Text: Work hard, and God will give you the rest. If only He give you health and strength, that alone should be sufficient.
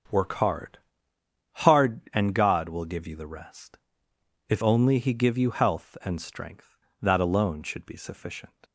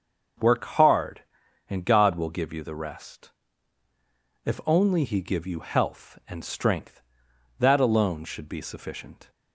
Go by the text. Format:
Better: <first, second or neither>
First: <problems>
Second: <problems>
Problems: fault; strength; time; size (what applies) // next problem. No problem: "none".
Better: second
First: starts louder than the rest; until 1.9 s; 7 dB // says "hard" twice; at 1.6 s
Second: starts louder than the rest; until 1.8 s; 6.5 dB